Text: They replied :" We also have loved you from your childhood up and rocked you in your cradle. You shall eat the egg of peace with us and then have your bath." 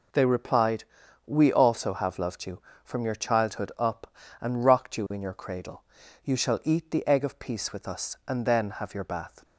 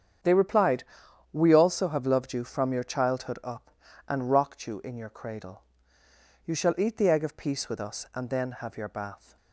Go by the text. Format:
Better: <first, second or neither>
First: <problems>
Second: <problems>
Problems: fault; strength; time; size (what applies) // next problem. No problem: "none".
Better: neither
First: none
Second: none